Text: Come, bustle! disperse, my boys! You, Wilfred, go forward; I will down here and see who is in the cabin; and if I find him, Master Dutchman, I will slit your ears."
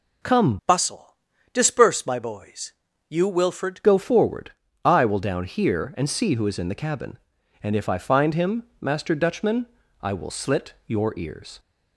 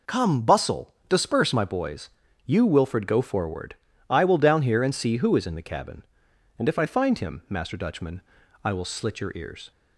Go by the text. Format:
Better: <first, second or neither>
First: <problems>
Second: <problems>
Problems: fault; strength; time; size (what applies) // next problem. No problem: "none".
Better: second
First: changes voice from "bustle" to "Wilfred"; from 0.6 to 3.8 s; 3.2 s long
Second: none